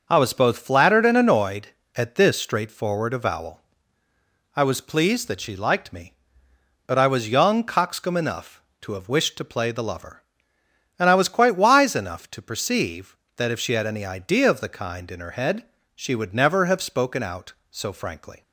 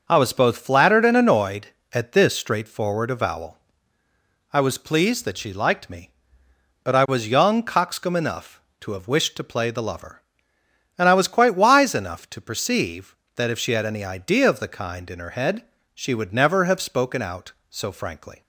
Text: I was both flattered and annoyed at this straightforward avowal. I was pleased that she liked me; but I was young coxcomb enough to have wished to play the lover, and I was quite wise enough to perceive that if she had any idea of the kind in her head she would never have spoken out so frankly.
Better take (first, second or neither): neither